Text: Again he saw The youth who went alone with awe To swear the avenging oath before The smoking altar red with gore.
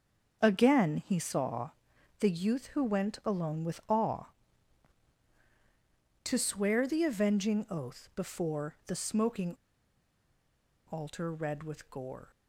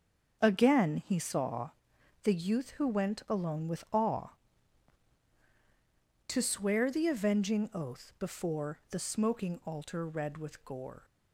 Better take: second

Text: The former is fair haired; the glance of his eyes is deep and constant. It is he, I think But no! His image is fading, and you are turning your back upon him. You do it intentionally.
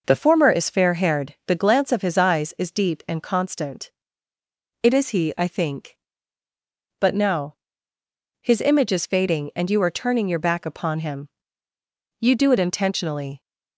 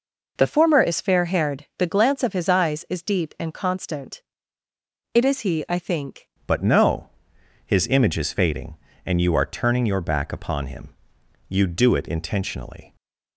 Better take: first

